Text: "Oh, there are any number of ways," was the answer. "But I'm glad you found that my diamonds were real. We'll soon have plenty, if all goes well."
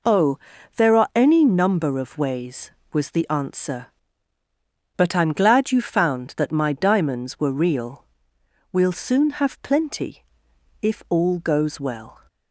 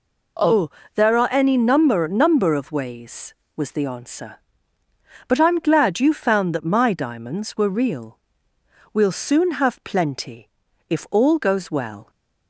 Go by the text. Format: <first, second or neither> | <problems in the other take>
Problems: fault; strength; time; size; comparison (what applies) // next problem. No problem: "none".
first | says "number" twice; at 2.0 s